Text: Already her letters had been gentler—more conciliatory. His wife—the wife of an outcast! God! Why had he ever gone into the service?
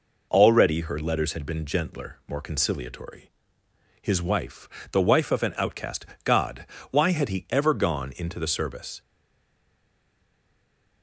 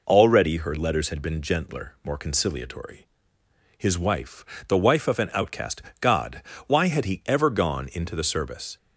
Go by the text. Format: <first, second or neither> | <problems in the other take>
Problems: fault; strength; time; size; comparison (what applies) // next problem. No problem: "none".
second | stays silent after the last word; noticeable; from 9.0 s on; 2.0 s long